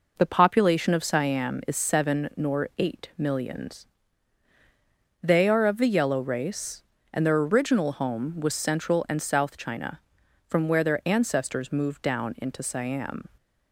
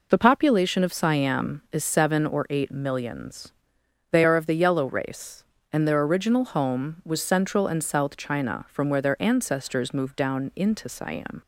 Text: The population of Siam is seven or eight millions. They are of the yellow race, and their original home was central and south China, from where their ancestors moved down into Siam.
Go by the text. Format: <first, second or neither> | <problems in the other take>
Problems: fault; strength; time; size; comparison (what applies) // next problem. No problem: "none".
second | says "nor" for "or"; at 2.3 s